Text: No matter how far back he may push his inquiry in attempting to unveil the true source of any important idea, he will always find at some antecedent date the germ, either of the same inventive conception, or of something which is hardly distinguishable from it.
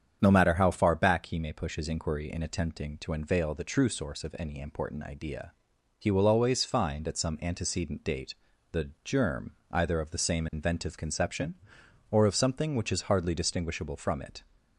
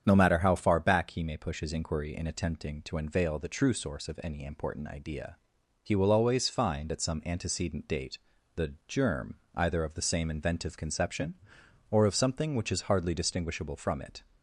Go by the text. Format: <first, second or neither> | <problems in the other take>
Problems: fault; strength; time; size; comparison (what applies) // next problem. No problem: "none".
neither | starts louder than the rest; strong; the same in both // pauses between "date" and "the"; the same in both